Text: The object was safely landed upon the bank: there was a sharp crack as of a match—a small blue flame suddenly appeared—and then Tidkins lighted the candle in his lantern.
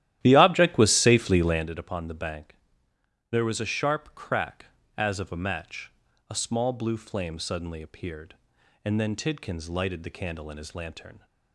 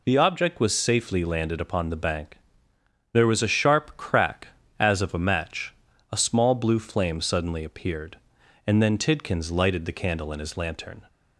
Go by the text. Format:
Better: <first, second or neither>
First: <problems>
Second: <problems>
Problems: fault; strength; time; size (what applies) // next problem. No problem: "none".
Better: second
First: starts louder than the rest; strong; until 1.7 s; 13 dB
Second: none